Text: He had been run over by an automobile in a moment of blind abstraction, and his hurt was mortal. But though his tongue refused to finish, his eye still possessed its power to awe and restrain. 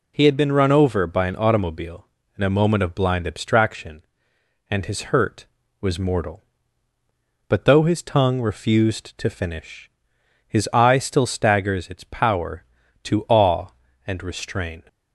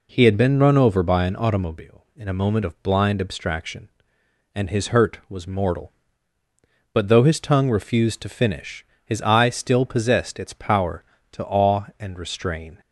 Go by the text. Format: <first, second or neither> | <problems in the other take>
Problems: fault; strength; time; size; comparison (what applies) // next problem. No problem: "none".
second | says "staggers" for "possessed"; at 11.2 s